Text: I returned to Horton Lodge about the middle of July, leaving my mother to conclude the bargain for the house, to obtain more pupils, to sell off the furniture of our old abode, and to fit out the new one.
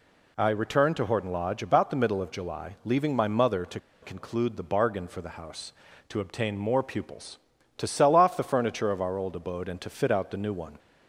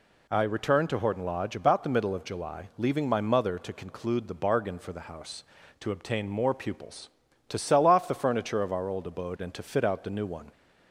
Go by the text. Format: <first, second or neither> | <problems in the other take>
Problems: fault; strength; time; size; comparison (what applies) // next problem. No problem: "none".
second | pauses between "to" and "conclude"; slight; at 3.7 s; 0.23 s long